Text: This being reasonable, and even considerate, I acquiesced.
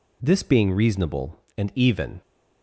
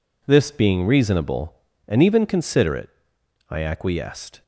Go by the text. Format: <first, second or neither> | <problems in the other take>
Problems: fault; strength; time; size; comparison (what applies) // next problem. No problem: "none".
second | stops before "considerate I acquiesced"; at 2.2 s